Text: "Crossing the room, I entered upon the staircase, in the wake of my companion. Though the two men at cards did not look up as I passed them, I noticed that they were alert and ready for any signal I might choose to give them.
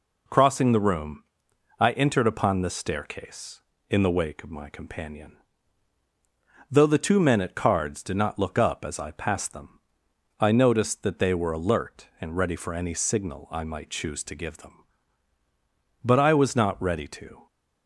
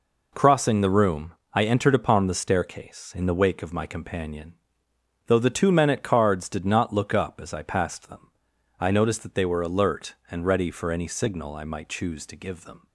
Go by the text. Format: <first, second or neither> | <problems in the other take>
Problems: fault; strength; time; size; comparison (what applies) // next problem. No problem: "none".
second | goes on to say "But I was not ready to"; from 16.0 s on; 1.4 s long